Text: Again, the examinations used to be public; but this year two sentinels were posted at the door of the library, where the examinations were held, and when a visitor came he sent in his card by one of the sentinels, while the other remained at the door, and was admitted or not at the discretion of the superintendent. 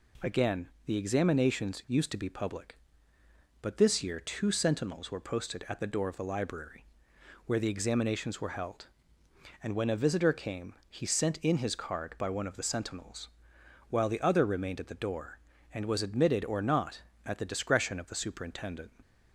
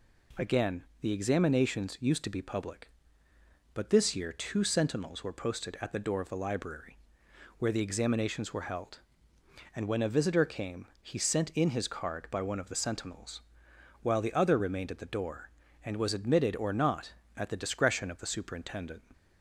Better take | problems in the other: neither | none

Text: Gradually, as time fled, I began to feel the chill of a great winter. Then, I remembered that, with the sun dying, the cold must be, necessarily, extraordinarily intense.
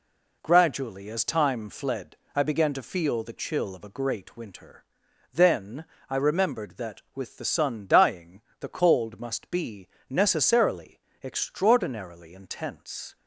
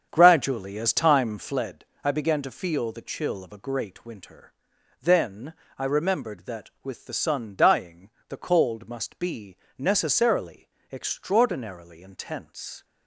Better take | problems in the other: first | starts louder than the rest; strong; until 1.7 s; 7.5 dB

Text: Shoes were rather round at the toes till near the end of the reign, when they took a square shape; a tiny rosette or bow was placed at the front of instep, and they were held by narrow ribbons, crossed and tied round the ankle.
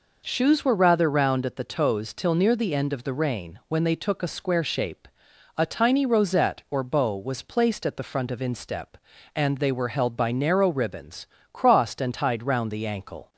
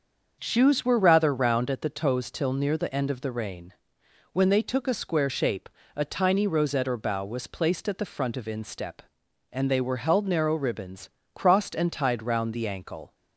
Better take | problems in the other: first | starts louder than the rest; until 1.4 s; 6.5 dB // skips "by"; at 10.2 s

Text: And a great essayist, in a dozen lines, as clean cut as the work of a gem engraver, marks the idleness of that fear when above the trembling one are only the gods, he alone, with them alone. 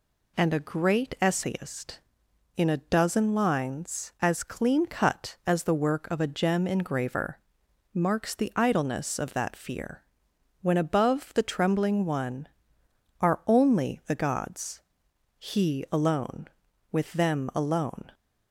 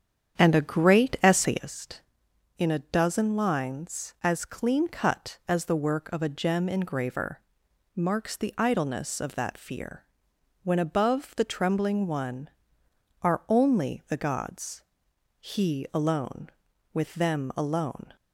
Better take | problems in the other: first | starts louder than the rest; strong; until 1.8 s; 8.5 dB // pauses between "fear" and "when"; noticeable; at 10.0 s; 0.60 s long; noticeable in the first

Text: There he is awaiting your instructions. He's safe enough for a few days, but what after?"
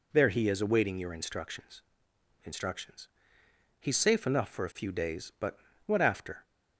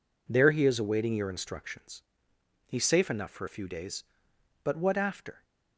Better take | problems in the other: second | says "instructions" twice; at 2.4 s // pauses between "but" and "what"; slight; at 5.5 s; 0.28 s long

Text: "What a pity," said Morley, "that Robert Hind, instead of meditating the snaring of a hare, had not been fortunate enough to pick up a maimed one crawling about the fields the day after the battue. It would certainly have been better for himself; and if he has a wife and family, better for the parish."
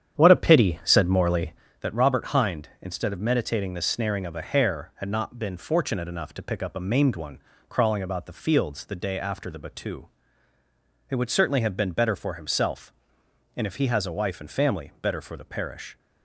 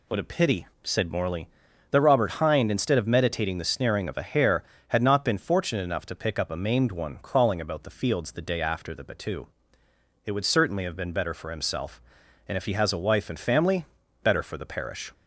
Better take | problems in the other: second | starts louder than the rest; strong; until 1.7 s; 9 dB // pauses between "one" and "crawling"; slight; at 7.3 s; 0.30 s long

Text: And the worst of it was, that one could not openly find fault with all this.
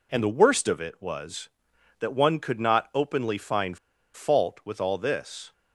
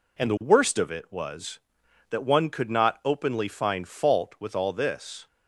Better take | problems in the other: second | pauses between "find" and "fault"; at 3.7 s; 0.37 s long

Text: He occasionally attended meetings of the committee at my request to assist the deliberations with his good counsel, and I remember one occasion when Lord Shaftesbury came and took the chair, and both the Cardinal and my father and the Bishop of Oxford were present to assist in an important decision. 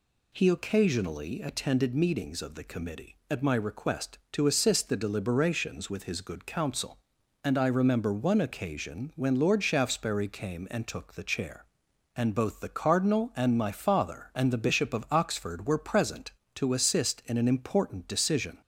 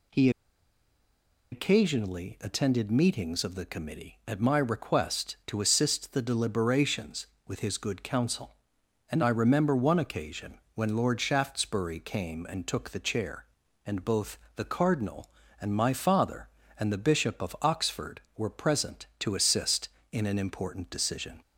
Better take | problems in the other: first | pauses between "He" and "occasionally"; at 0.2 s; 1.2 s long // pauses between "both" and "the"; slight; at 14.3 s; 0.16 s long

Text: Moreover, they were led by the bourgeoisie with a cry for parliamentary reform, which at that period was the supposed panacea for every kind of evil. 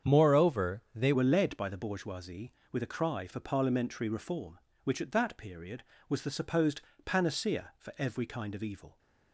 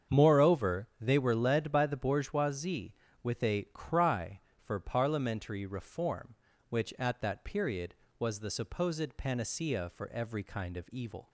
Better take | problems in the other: second | starts louder than the rest; strong; until 1.1 s; 8 dB; strong in the second // changes voice at "were"; from 1.1 s on; 7.8 s long // pauses between "supposed" and "panacea"; slight; at 6.8 s; 0.24 s long

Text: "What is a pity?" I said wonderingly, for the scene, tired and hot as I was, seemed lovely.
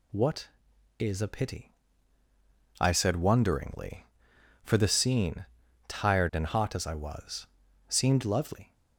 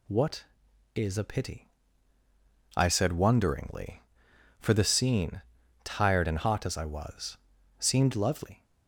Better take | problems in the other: neither | none

